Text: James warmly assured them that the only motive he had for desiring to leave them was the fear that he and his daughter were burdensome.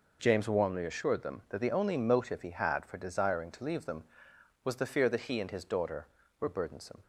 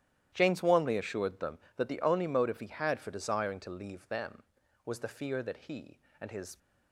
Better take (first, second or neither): first